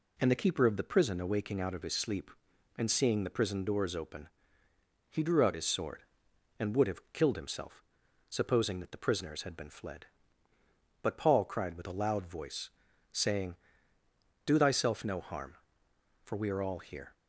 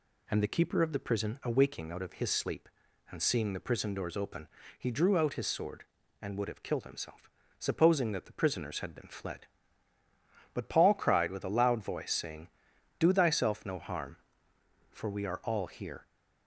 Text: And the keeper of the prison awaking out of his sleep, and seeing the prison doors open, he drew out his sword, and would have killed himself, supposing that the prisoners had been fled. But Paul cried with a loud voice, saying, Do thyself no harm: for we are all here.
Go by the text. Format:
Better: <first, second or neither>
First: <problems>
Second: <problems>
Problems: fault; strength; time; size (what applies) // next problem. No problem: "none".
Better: neither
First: none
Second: none